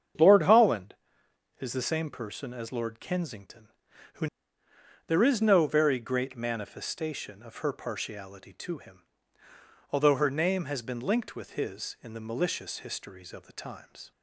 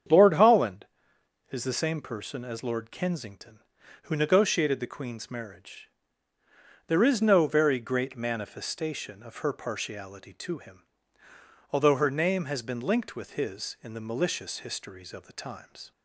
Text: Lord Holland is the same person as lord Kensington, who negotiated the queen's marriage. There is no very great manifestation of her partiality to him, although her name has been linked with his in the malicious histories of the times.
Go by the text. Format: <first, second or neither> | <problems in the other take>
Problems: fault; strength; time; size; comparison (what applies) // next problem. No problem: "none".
second | starts louder than the rest; strong; until 1.8 s; 8 dB; strong in the second // skips "negotiated the queen's marriage"; at 4.6 s